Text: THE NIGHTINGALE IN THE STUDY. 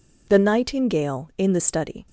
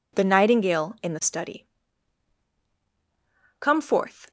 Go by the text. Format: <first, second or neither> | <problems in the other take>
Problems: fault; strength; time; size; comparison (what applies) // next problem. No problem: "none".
first | goes on to say "Come forth"; noticeable; from 3.5 s on; 0.70 s long